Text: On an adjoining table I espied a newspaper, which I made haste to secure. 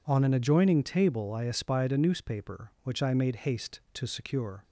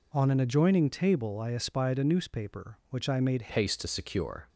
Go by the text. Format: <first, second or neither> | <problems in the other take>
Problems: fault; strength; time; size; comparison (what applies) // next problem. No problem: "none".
first | changes voice at "haste"; from 3.5 s on; 0.9 s long